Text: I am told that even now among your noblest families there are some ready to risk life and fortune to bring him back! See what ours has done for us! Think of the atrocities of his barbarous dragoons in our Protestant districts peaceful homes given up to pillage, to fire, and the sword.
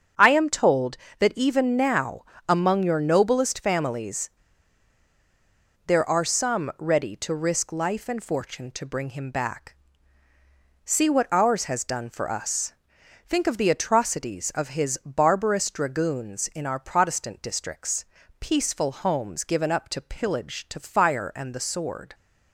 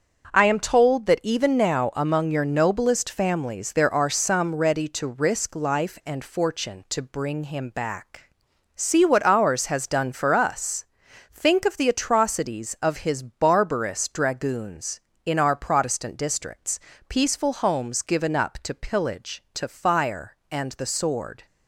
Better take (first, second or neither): second